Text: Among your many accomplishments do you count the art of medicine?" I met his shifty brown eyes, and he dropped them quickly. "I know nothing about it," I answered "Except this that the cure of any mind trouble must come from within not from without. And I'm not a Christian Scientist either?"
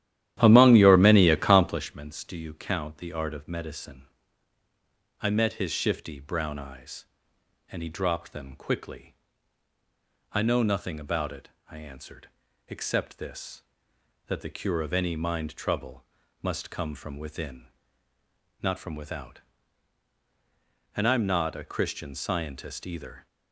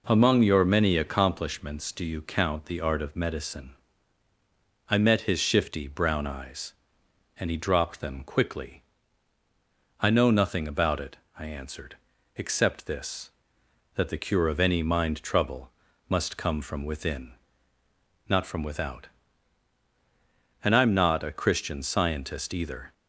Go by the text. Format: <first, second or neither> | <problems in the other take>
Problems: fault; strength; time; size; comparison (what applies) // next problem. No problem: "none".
second | starts louder than the rest; strong; until 2.0 s; 12 dB // pauses between "answered" and "Except"; at 12.2 s; 0.38 s long; also in the second // pauses between "trouble" and "must"; at 16.0 s; 0.38 s long; also in the second // pauses between "within" and "not"; noticeable; at 17.6 s; 0.94 s long; noticeable in the second